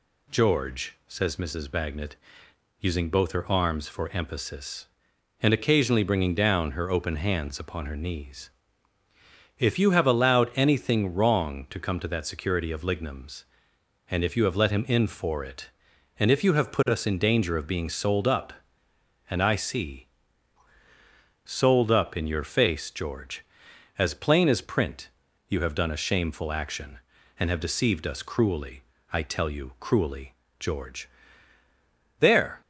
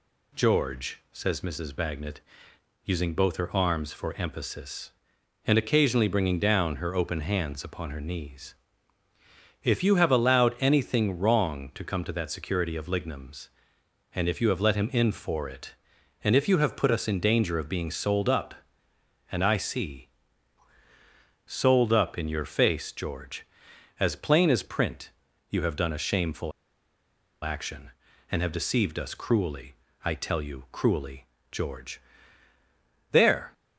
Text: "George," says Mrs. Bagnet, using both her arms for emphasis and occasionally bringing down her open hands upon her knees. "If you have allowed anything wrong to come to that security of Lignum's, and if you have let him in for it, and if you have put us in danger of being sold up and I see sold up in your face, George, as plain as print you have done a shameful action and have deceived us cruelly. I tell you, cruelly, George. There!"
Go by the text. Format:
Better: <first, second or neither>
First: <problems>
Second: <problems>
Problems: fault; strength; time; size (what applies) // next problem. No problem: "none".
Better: first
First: pauses between "see" and "sold"; strong; at 20.0 s; 1.3 s long // pauses between "print" and "you"; at 25.0 s; 0.40 s long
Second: pauses between "see" and "sold"; strong; at 20.0 s; 1.3 s long // pauses between "print" and "you"; at 25.1 s; 0.40 s long // pauses between "shameful" and "action"; noticeable; at 26.5 s; 0.93 s long